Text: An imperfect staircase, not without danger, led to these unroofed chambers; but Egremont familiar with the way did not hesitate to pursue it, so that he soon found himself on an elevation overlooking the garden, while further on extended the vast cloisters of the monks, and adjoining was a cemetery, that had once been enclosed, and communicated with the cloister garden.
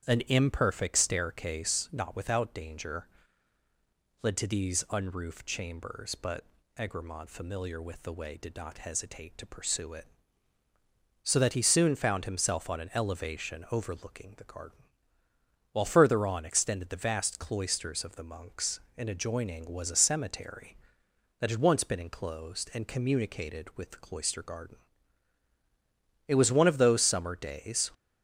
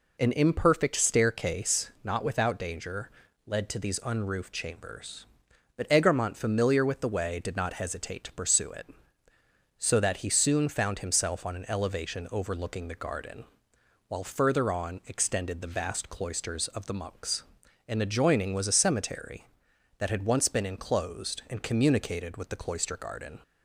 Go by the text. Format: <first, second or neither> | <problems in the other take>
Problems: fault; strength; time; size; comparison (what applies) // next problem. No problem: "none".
second | starts louder than the rest; strong; until 1.0 s; 9 dB // pauses between "but" and "Egremont"; slight; at 6.4 s; 0.34 s long // goes on to say "It was one of those summer days"; from 26.2 s on; 1.6 s long